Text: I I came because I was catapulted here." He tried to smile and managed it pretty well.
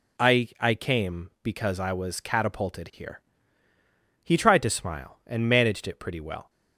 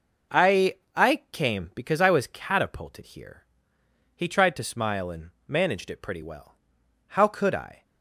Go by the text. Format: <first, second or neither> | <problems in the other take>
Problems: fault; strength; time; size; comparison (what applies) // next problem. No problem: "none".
first | pauses between "I" and "I"; slight; at 0.7 s; 0.20 s long // pauses between "and" and "managed"; slight; at 5.3 s; 0.16 s long // goes on to say "How could I"; noticeable; from 7.0 s on; 0.78 s long